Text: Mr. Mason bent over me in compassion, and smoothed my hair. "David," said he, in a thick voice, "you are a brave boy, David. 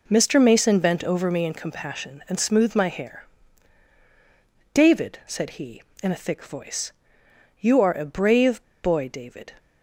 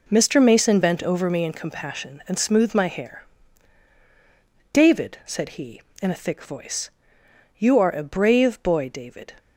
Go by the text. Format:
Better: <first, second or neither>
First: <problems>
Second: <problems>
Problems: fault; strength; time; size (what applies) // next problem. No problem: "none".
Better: second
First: pauses between "brave" and "boy"; slight; at 8.6 s; 0.18 s long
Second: none